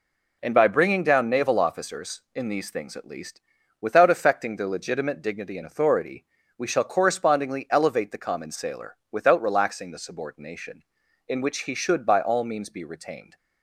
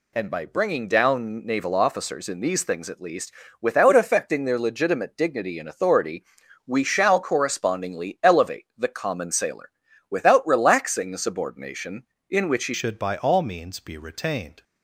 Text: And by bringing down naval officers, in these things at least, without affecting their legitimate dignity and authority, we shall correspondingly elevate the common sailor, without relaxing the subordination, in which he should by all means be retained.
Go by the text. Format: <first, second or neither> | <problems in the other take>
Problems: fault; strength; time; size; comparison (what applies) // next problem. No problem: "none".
first | changes voice at "should"; from 12.7 s on; 1.9 s long